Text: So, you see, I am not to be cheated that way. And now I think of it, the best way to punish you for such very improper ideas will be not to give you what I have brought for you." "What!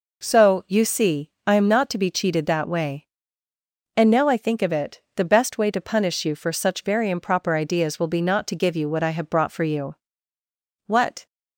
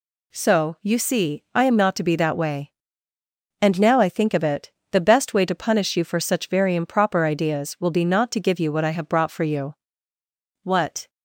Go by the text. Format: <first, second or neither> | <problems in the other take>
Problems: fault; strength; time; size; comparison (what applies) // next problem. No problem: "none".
first | skips "cheated"; at 2.1 s